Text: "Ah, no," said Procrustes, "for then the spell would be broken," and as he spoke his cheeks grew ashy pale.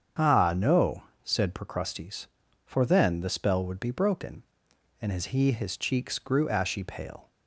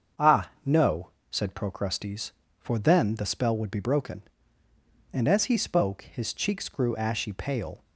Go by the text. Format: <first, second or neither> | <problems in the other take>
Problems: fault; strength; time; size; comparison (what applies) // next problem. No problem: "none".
second | starts louder than the rest; strong; until 1.4 s; 7.5 dB; also in the second // skips "spoke"; at 5.5 s